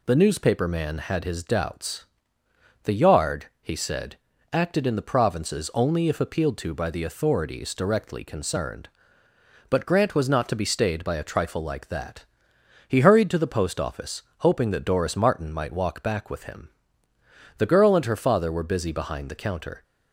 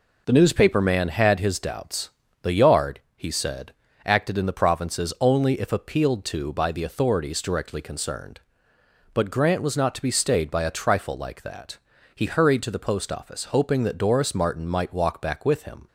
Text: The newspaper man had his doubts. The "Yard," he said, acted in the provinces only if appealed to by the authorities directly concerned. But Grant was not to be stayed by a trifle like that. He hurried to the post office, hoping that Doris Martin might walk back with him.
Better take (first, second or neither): second